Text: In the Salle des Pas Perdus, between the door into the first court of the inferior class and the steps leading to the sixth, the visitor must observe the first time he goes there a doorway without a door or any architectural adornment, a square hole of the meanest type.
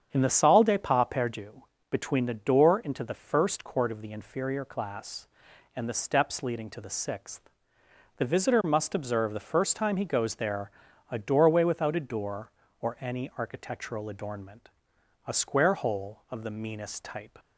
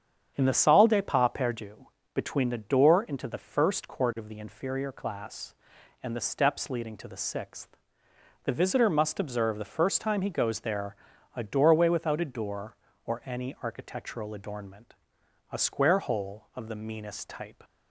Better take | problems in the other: neither | starts louder than the rest; strong; the same in both // pauses between "there" and "a"; the same in both

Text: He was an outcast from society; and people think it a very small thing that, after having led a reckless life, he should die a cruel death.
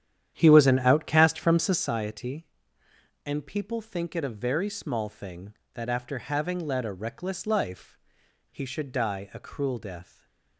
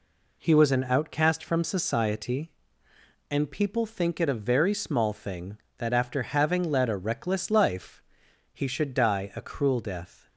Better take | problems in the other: second | starts louder than the rest; strong; until 2.0 s; 10 dB // stays silent after the last word; slight; from 10.0 s on; 0.5 s long

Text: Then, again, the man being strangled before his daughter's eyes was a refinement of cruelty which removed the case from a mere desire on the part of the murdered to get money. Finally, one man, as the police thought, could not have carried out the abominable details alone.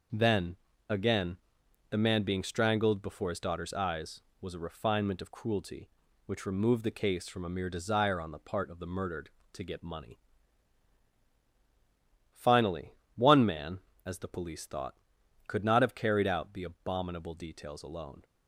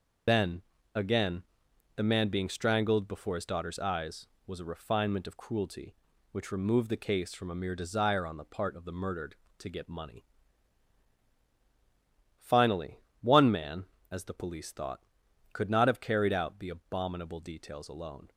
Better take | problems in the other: first | loses the start of "Then"; at 0.2 s; 100 ms

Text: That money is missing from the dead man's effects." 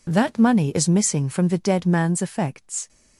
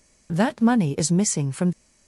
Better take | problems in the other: first | stops before "the dead man's effects"; at 1.7 s

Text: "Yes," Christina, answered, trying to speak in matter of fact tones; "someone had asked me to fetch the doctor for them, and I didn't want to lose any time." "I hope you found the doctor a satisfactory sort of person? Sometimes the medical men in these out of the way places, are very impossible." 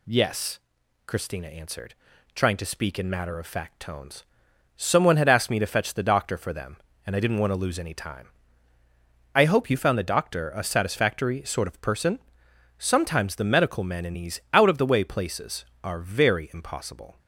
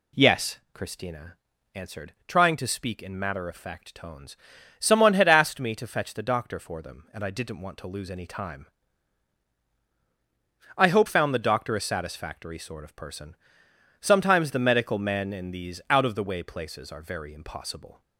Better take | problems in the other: first | skips "you"; at 11.0 s

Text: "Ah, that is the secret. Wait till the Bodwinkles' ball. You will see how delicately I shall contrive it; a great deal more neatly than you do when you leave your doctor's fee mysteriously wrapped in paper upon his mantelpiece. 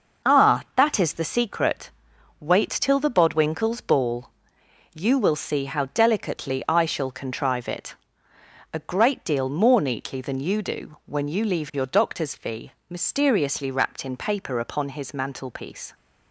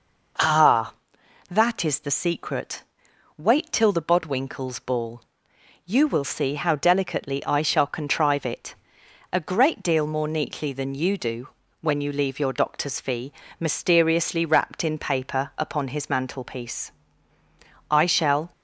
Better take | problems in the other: first | pauses between "do" and "when"; slight; at 11.4 s; 0.34 s long // pauses between "fee" and "mysteriously"; slight; at 13.3 s; 0.26 s long; slight in the first // goes on to say "I shall"; noticeable; from 17.8 s on; 0.62 s long

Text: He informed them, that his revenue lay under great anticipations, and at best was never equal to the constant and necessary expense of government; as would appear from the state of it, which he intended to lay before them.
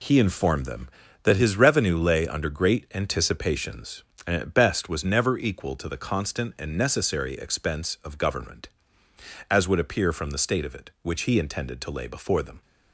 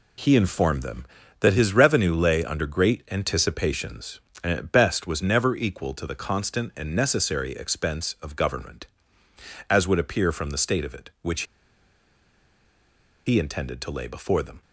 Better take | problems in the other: first | pauses between "which" and "he"; strong; at 11.4 s; 1.8 s long

